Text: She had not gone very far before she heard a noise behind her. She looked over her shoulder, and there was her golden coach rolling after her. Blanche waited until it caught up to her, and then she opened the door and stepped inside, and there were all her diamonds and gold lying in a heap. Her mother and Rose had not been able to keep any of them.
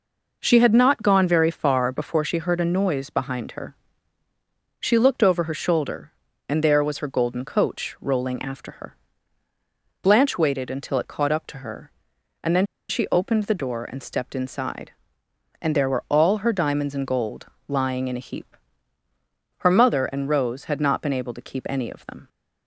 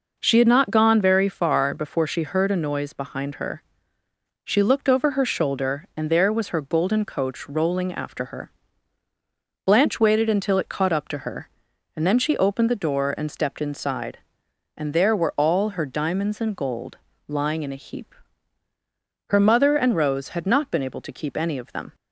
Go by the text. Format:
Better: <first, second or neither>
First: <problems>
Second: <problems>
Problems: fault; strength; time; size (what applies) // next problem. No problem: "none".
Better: second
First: pauses between "then" and "she"; slight; at 12.6 s; 0.24 s long // pauses between "gold" and "lying"; slight; at 17.4 s; 0.20 s long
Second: pauses between "gold" and "lying"; slight; at 16.9 s; 0.30 s long